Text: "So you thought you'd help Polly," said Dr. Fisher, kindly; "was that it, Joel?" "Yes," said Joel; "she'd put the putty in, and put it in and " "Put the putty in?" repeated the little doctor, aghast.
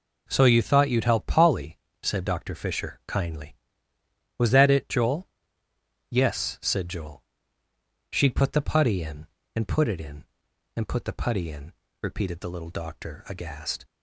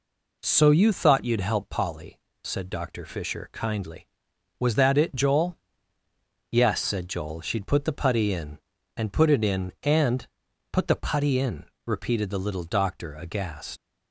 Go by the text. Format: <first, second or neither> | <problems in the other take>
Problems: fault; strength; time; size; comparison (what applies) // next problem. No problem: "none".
first | leaves "aghast" unfinished; at 13.7 s; 120 ms